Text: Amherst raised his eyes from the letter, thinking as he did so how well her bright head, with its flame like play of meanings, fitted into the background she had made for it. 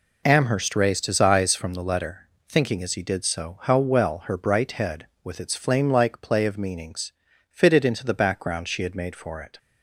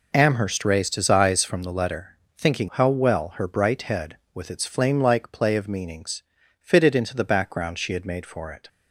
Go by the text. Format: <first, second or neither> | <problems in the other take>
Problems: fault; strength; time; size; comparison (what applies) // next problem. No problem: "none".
first | skips "as he did so"; at 2.7 s